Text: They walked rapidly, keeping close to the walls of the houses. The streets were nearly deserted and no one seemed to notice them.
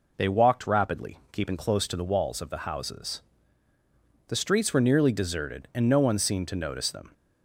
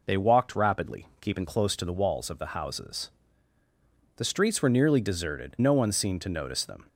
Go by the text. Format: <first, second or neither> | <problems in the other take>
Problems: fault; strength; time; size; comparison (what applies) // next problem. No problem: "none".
first | skips "and"; at 5.5 s